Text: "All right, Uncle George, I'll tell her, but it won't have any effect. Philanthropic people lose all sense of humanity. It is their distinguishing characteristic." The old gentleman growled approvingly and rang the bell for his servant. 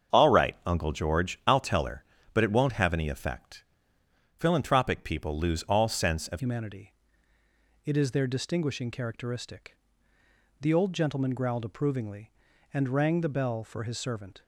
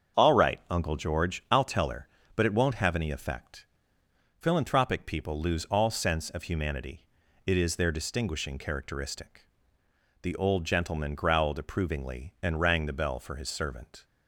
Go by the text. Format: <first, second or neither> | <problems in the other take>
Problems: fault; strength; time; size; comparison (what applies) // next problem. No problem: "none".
second | starts louder than the rest; strong; until 1.2 s; 7.5 dB; strong in the second // changes voice at "humanity"; from 6.3 s on; 8.1 s long